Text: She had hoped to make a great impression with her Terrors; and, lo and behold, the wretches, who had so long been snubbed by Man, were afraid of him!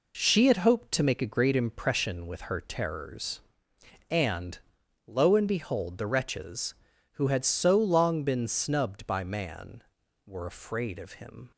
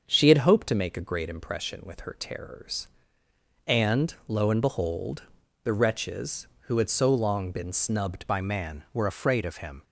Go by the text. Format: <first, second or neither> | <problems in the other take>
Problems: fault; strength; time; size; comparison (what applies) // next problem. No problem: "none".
first | starts louder than the rest; until 1.0 s; 6.5 dB // changes voice at "by"; from 8.2 s on; 1.6 s long